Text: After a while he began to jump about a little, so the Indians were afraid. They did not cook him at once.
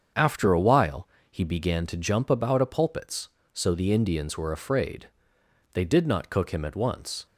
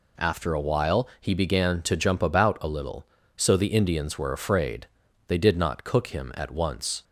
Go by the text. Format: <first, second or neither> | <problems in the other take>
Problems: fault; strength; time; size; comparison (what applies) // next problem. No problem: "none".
second | starts louder than the rest; strong; until 1.4 s; 7 dB // pauses between "while" and "he"; slight; at 1.0 s; 0.24 s long // says "pulpits" for "little"; at 2.6 s